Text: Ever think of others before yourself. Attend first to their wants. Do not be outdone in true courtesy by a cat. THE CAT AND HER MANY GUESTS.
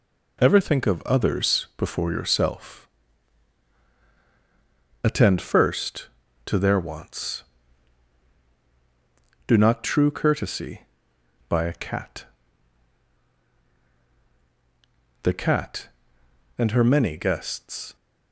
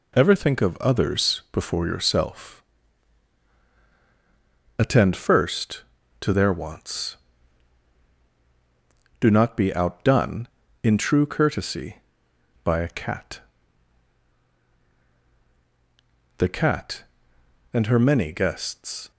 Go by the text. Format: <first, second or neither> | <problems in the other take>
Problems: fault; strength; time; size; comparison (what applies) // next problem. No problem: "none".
second | skips "be outdone in"; at 9.8 s